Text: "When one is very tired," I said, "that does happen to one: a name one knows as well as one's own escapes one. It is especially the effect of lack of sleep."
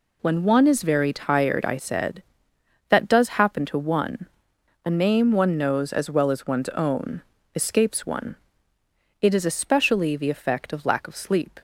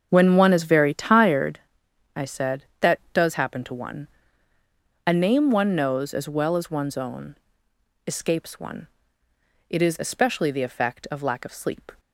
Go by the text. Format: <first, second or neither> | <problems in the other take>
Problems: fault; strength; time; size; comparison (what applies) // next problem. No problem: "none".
first | starts louder than the rest; until 1.4 s; 7 dB // pauses between "own" and "escapes"; noticeable; at 7.3 s; 0.70 s long; slight in the first